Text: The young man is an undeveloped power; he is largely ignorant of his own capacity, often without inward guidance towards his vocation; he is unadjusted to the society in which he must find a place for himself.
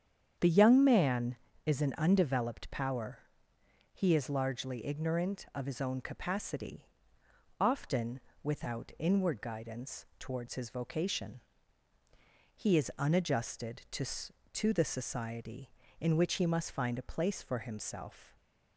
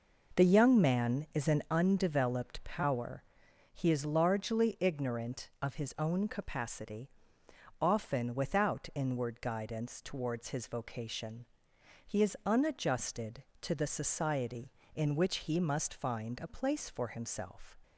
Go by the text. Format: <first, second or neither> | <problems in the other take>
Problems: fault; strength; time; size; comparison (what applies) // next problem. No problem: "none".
second | starts louder than the rest; strong; until 1.7 s; 8.5 dB // pauses between "often" and "without"; slight; at 8.1 s; 0.24 s long // says "to" twice; at 14.5 s